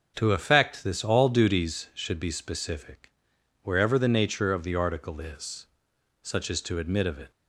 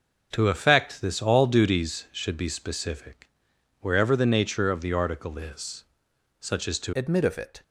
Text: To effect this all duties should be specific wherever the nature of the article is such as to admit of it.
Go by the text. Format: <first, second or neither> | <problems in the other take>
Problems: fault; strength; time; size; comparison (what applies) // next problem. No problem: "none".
first | pauses between "specific" and "wherever"; noticeable; at 3.2 s; 0.52 s long; noticeable in the first // pauses between "is" and "such"; noticeable; at 5.8 s; 0.56 s long; noticeable in the first // changes voice at "admit"; from 6.9 s on; 0.7 s long